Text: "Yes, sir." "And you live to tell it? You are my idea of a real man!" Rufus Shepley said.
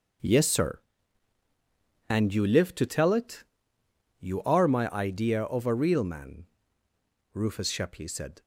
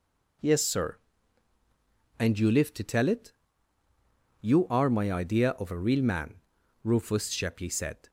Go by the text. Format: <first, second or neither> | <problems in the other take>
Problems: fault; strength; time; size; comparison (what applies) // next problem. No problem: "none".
second | gets quieter; strong; throughout; 10.5 dB